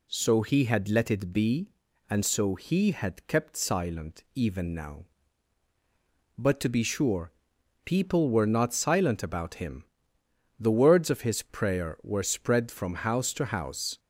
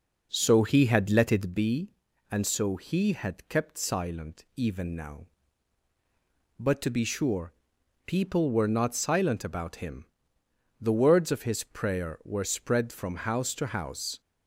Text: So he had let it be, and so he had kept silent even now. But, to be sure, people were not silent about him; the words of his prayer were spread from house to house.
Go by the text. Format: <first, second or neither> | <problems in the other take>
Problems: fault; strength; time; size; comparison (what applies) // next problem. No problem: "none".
first | starts louder than the rest; noticeable; until 1.6 s; 5 dB